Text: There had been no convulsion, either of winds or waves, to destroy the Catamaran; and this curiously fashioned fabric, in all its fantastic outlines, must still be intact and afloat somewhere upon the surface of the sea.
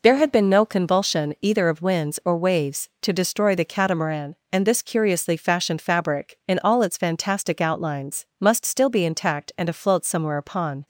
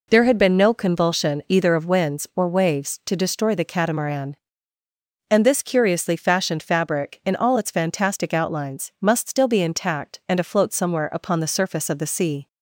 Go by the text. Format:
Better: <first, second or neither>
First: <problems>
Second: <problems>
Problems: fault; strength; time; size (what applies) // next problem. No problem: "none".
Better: second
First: stops before "the surface of the sea"; at 10.8 s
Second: none